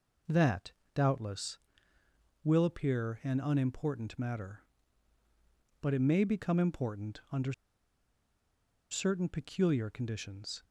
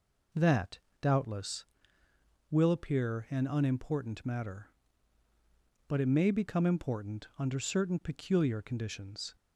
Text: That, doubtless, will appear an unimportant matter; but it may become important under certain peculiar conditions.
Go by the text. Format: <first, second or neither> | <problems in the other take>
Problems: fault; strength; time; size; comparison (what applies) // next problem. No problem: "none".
second | pauses between "under" and "certain"; strong; at 7.5 s; 1.3 s long